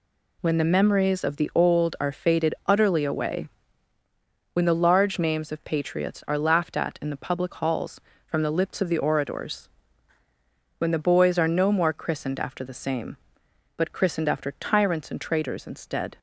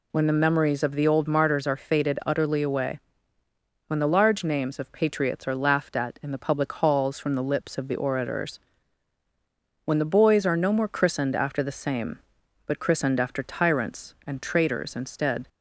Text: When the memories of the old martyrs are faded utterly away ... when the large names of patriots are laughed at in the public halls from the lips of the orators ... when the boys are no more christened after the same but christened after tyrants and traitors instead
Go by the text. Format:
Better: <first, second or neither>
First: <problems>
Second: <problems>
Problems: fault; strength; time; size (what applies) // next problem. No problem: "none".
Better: second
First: skips "martyrs"; at 1.9 s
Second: none